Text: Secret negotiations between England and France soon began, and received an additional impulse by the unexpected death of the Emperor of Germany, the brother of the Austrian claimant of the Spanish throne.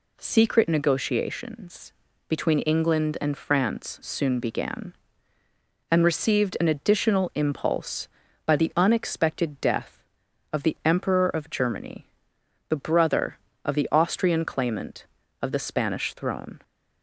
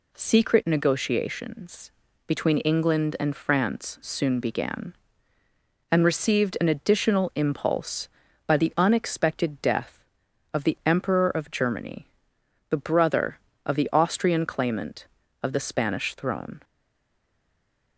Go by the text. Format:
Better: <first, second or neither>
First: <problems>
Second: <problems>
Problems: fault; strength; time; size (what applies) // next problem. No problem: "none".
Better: first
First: pauses between "negotiations" and "between"; at 1.9 s; 0.38 s long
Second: pauses between "negotiations" and "between"; at 1.8 s; 0.38 s long // stays silent after the last word; noticeable; from 16.6 s on; 1.3 s long